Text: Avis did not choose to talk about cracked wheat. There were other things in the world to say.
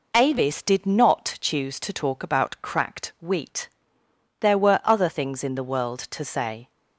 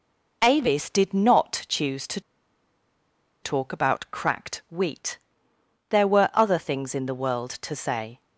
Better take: first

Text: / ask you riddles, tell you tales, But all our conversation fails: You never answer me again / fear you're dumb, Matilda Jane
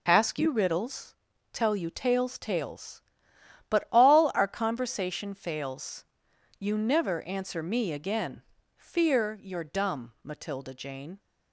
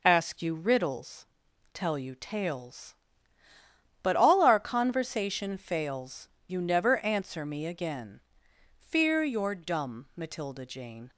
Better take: second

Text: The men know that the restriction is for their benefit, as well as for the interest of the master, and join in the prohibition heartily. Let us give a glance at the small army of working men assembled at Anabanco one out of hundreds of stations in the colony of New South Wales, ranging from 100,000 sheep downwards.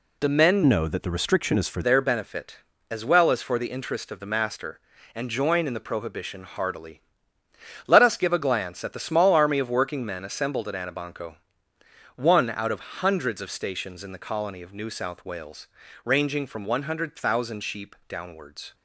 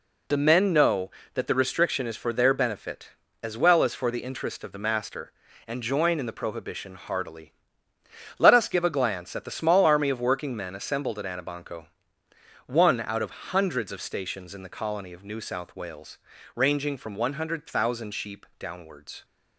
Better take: second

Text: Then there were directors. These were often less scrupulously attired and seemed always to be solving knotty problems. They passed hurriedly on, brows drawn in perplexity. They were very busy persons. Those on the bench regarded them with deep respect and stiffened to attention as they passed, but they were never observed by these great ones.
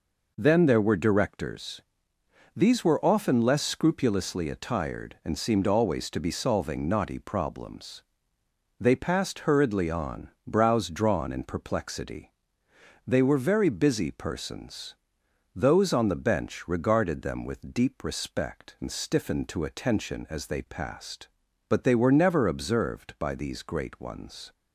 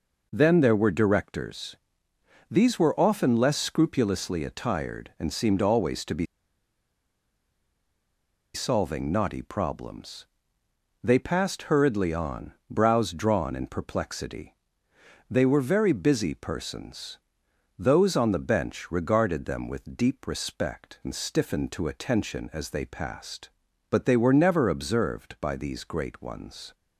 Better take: first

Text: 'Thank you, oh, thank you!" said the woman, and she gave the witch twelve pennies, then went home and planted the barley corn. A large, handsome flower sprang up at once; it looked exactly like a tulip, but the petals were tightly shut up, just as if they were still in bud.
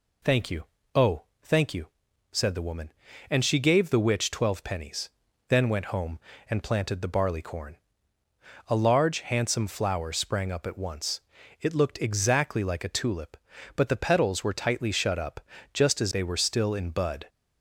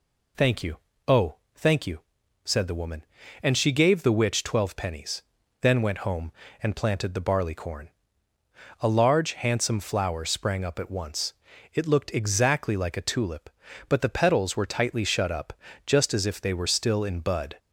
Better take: second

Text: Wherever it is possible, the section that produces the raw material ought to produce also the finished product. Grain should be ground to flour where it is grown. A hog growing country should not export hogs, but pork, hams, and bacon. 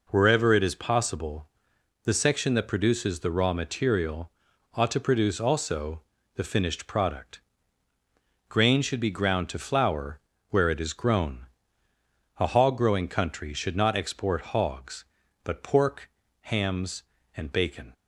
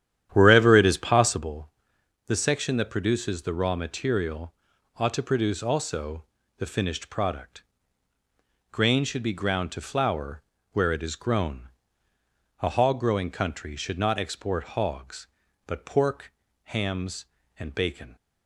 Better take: first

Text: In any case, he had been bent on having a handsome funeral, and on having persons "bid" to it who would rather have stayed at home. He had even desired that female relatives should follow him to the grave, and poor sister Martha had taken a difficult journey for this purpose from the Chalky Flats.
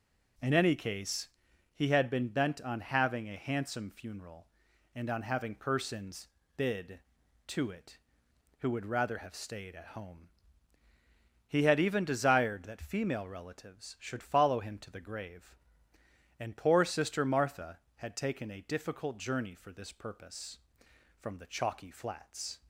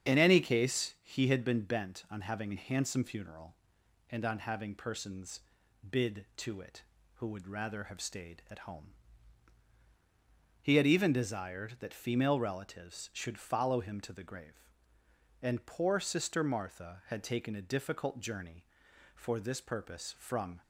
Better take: first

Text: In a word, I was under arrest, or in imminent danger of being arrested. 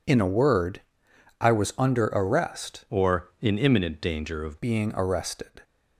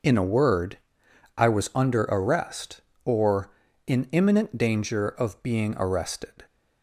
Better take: second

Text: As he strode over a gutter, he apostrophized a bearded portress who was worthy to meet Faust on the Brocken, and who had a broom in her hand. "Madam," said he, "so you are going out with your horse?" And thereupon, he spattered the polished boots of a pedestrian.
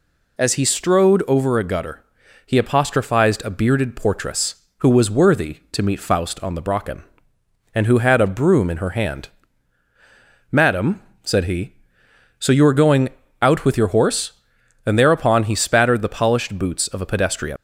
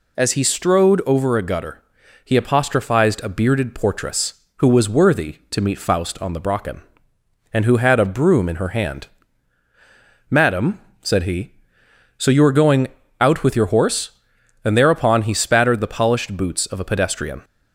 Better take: second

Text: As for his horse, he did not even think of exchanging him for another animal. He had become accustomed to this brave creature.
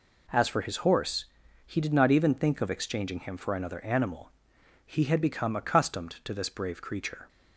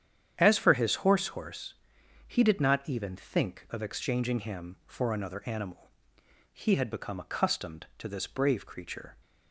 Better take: first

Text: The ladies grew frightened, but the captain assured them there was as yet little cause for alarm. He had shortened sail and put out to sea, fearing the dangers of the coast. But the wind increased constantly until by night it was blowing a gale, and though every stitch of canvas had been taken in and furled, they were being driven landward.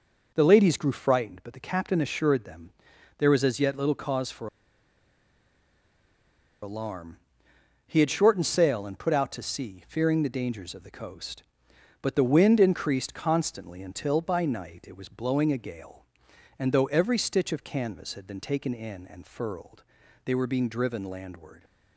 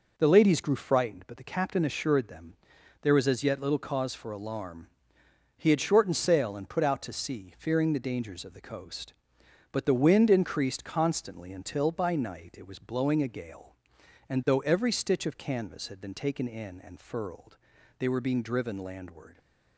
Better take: second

